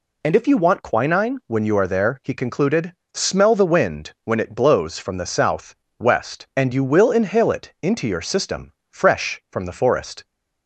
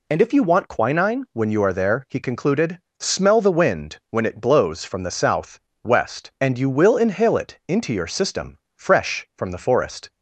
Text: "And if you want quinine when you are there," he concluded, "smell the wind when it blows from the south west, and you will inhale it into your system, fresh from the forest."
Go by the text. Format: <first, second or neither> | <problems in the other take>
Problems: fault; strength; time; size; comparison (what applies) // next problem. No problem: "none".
neither | pauses between "south" and "west"; slight; the same in both